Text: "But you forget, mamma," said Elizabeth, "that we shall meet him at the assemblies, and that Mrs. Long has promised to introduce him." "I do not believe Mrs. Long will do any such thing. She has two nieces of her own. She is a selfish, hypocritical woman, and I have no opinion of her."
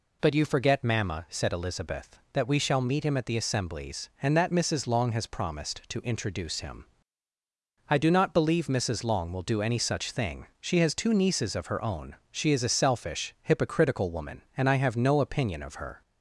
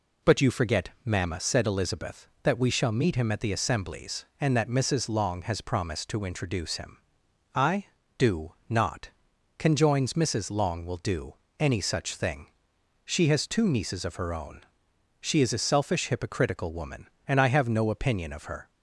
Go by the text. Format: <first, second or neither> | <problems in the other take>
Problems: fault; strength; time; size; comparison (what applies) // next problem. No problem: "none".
first | pauses between "do" and "not"; slight; at 8.5 s; 0.16 s long // says "conjoins" for "believe"; at 9.5 s // pauses between "do" and "any"; slight; at 11.3 s; 0.24 s long